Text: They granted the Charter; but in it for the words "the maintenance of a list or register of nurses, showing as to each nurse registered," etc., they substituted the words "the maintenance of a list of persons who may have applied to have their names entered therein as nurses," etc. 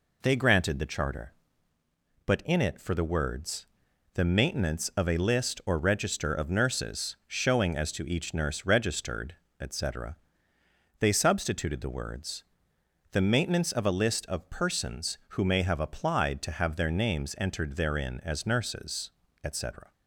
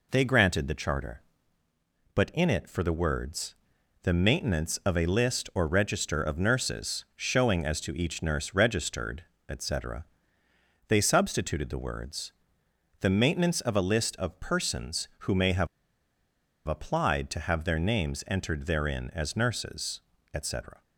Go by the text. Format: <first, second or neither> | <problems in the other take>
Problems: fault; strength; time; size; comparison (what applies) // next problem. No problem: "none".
first | pauses between "words" and "the"; noticeable; at 3.5 s; 0.50 s long; noticeable in the first // pauses between "words" and "the"; noticeable; at 12.3 s; 0.68 s long; noticeable in the first // pauses between "have" and "applied"; at 15.6 s; 0.99 s long